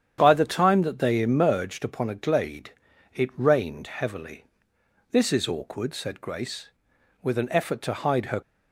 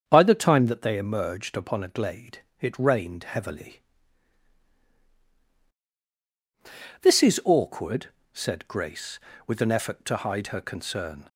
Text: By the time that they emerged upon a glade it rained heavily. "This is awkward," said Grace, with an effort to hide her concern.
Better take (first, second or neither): second